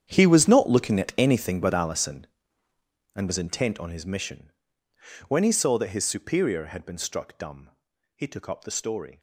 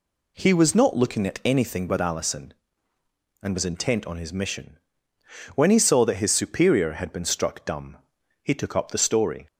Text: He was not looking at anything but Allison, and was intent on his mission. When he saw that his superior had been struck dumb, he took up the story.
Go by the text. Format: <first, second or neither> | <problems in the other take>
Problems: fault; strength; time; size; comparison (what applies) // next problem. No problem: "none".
second | gets quieter; strong; throughout; 16 dB